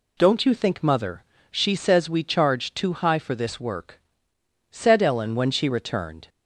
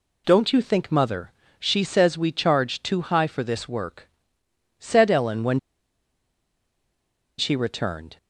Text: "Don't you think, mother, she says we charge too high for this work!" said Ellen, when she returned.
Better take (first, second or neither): first